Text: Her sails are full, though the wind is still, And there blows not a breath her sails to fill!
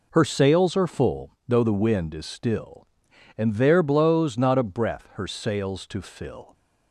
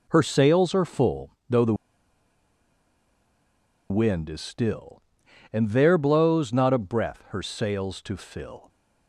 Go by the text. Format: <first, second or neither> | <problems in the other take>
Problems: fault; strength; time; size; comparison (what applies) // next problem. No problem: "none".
first | pauses between "the" and "wind"; strong; at 1.7 s; 2.1 s long